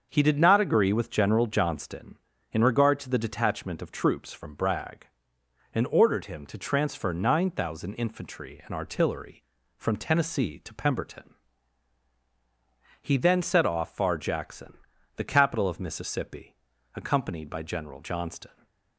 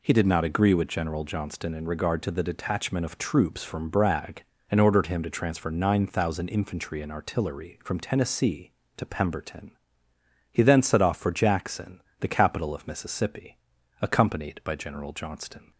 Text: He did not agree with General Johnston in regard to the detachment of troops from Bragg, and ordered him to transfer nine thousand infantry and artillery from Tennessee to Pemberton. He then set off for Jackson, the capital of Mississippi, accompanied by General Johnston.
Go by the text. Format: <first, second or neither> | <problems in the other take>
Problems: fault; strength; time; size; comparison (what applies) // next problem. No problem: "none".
second | starts louder than the rest; until 1.1 s; 6.5 dB // says "far" for "for"; at 13.9 s